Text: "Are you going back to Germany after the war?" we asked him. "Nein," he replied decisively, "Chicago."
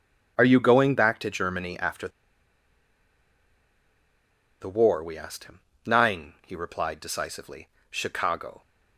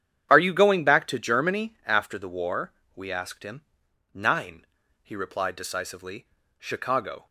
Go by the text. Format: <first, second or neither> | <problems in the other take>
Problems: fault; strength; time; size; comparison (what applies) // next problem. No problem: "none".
second | starts louder than the rest; strong; until 1.3 s; 9.5 dB; strong in the second // pauses between "after" and "the"; strong; at 2.0 s; 2.5 s long